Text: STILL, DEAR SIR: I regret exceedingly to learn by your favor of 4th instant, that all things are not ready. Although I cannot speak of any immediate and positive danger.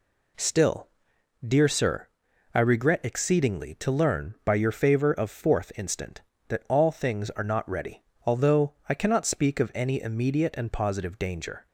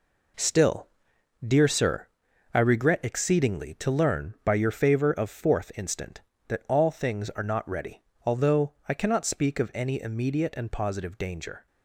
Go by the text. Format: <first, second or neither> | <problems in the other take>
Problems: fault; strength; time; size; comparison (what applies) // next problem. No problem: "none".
first | gets quieter; strong; throughout; 8.5 dB // pauses between "Although" and "I"; slight; at 8.7 s; 0.16 s long; slight in the first